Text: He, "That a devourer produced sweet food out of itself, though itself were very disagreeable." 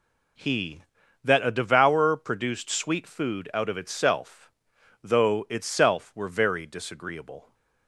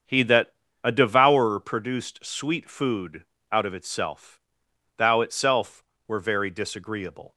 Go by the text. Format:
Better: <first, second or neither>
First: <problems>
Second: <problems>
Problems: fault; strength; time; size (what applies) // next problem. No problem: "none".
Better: first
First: none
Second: starts louder than the rest; strong; until 1.3 s; 7.5 dB // pauses between "That" and "a"; slight; at 0.5 s; 0.32 s long // pauses between "food" and "out"; slight; at 3.2 s; 0.26 s long // says "thou" for "though"; at 4.9 s